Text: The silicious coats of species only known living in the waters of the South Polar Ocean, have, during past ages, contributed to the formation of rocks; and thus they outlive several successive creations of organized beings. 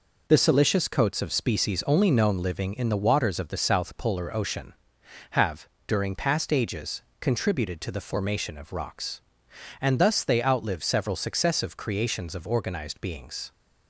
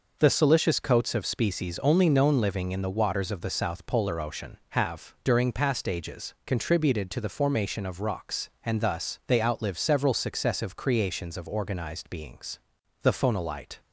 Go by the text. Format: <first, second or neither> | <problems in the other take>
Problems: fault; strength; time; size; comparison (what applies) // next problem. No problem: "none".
first | goes on to say "The phonolite"; noticeable; from 13.0 s on; 0.78 s long